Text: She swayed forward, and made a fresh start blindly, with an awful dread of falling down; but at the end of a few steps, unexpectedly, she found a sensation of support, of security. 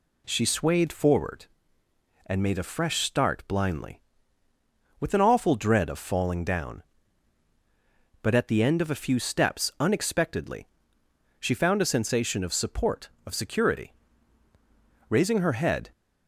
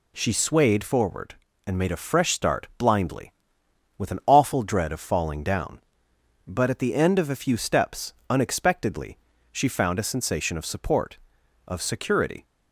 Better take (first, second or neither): second